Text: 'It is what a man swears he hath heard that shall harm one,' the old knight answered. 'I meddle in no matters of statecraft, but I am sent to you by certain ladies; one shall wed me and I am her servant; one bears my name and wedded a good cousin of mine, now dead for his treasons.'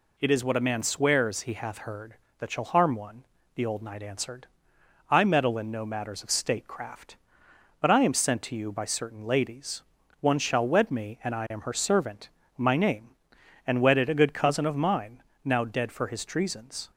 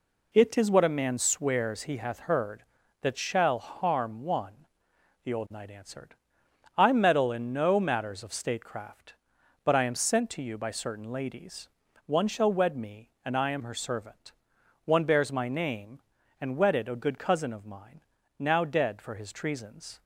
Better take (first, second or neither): second